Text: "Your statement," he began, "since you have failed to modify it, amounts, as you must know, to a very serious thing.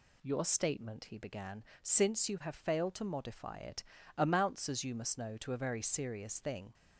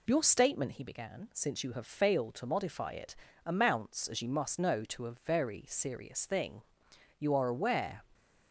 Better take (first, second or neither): first